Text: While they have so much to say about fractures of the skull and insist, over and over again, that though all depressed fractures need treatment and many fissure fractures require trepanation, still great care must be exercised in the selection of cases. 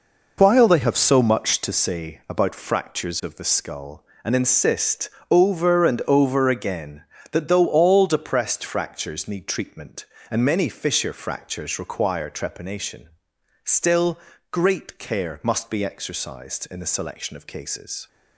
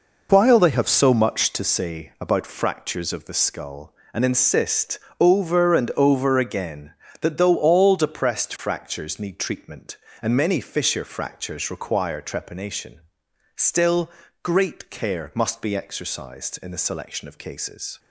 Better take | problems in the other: neither | pauses between "still" and "great"; slight; the same in both

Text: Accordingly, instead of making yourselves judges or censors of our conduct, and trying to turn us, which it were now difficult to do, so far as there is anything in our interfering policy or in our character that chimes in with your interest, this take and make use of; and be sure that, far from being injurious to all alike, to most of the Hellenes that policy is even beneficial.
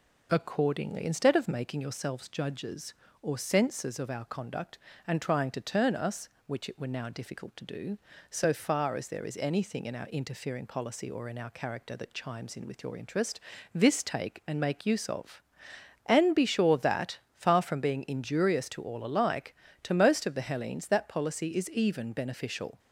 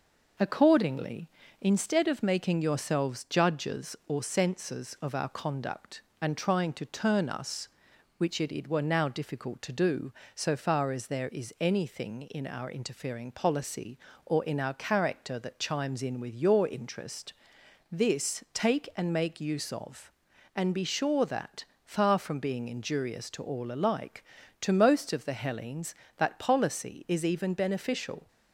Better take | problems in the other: first | says "it" twice; at 8.5 s

